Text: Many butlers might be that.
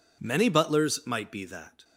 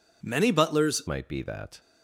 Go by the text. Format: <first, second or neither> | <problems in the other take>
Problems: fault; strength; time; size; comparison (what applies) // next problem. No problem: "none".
first | changes voice at "might"; from 1.0 s on; 0.7 s long